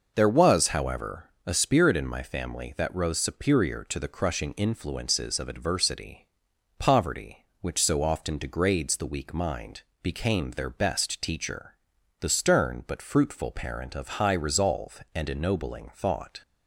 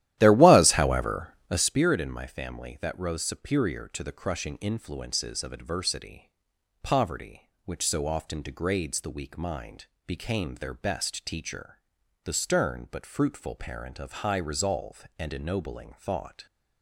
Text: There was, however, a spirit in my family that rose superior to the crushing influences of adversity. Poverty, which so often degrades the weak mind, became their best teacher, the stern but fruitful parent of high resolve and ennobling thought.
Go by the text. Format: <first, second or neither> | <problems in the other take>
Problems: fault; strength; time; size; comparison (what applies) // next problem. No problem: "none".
first | starts louder than the rest; strong; until 1.8 s; 13 dB